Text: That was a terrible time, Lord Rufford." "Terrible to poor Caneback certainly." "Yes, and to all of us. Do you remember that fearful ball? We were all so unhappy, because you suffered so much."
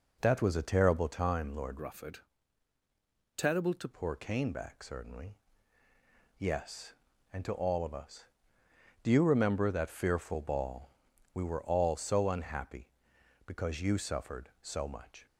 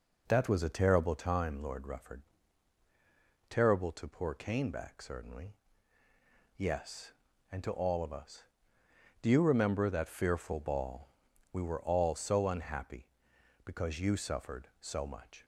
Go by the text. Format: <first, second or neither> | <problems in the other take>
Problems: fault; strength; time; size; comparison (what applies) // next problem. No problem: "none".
second | changes voice from "Rufford" to "to"; from 1.8 to 3.8 s; 2.0 s long